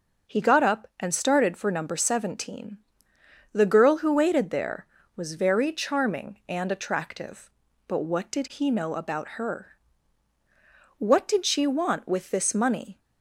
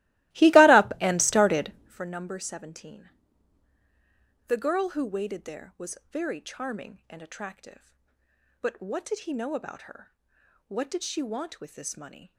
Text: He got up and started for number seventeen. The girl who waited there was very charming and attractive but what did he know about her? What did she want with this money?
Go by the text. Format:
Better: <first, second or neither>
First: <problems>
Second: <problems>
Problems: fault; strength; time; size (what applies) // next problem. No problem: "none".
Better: first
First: none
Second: starts louder than the rest; strong; until 2.0 s; 18 dB